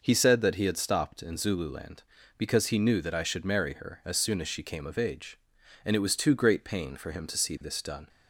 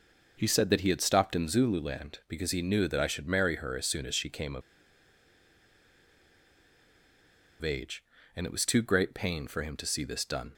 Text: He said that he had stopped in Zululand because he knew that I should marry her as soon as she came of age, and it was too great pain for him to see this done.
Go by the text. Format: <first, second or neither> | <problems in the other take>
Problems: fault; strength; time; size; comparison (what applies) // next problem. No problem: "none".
first | pauses between "of" and "age"; strong; at 4.6 s; 3.0 s long